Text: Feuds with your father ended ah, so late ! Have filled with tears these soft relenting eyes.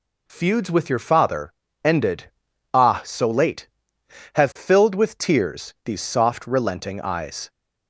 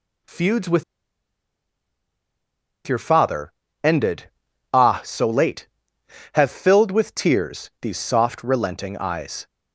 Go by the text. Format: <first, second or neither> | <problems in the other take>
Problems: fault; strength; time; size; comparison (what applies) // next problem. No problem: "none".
first | pauses between "with" and "your"; strong; at 0.8 s; 2.0 s long // pauses between "father" and "ended"; slight; at 3.5 s; 0.32 s long; slight in the first // pauses between "ended" and "ah"; at 4.2 s; 0.42 s long; also in the first